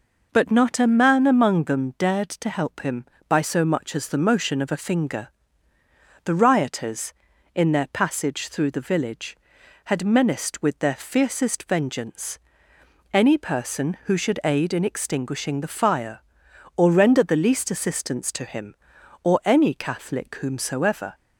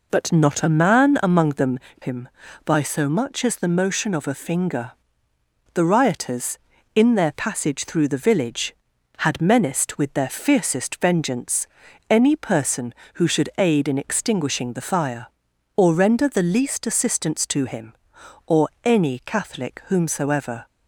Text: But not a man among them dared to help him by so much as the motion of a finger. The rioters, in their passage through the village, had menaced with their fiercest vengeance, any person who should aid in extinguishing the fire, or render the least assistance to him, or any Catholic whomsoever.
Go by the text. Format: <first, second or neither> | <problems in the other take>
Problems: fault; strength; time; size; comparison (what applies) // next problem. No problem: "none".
first | skips "dared to help"; at 1.9 s // pauses between "or" and "any"; slight; at 18.6 s; 0.16 s long